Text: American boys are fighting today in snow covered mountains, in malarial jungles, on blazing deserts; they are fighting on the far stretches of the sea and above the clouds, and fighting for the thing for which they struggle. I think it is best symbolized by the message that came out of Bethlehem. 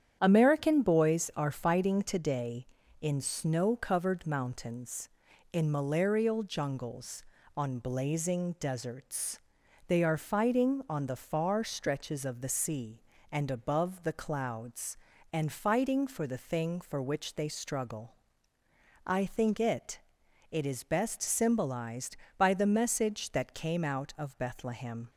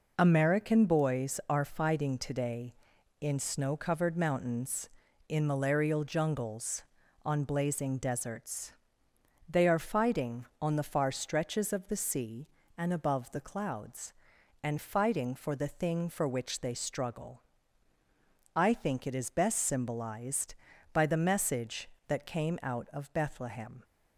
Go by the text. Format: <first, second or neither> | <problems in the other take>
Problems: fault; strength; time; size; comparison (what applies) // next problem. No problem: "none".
second | starts louder than the rest; strong; until 1.2 s; 9 dB // says "it" twice; at 20.5 s